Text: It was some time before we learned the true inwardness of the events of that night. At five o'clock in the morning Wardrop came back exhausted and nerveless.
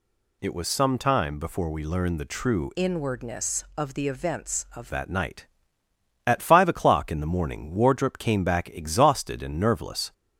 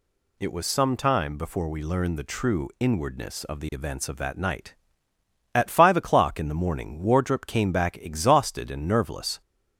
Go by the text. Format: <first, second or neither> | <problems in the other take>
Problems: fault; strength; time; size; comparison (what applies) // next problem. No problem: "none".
second | changes voice from "inwardness" to "of"; from 2.7 to 4.9 s; 2.2 s long